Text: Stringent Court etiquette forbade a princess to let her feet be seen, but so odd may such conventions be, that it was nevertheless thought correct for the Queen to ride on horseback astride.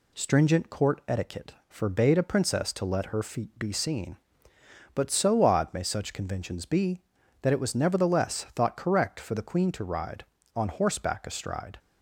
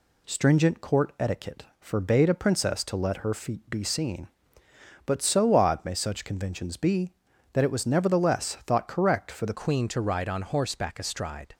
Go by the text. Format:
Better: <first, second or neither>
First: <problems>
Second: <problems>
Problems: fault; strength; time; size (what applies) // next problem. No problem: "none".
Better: first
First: none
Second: changes voice at "Queen"; from 9.5 s on; 2.0 s long